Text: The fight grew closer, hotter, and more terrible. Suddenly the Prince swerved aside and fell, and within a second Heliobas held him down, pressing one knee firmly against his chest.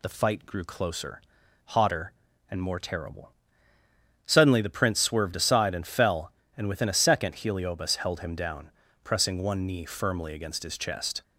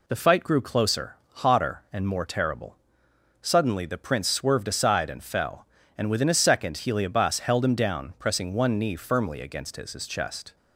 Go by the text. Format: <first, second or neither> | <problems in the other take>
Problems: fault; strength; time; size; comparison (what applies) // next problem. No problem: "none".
first | says "his" twice; at 9.9 s